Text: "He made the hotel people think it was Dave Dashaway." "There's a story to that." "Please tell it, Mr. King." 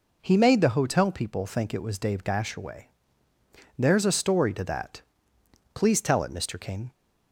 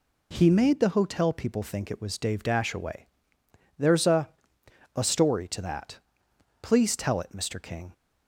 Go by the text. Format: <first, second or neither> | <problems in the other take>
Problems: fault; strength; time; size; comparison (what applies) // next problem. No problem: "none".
first | says "a" twice; at 4.9 s